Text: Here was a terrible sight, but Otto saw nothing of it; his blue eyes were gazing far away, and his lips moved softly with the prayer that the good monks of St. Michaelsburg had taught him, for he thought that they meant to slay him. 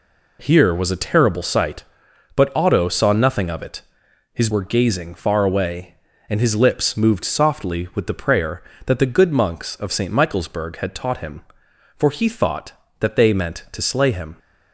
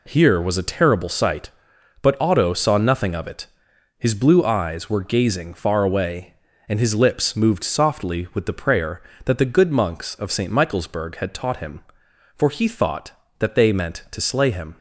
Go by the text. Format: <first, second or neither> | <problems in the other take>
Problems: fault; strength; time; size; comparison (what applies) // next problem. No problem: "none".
second | skips "blue eyes"; at 4.4 s